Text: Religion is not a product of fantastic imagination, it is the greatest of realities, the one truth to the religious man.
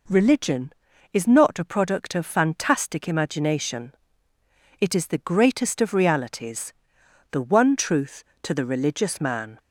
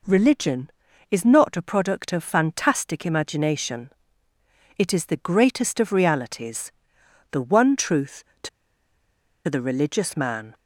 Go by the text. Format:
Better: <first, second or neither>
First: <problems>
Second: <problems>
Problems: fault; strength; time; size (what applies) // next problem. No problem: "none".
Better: first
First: none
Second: pauses between "to" and "the"; at 8.4 s; 0.98 s long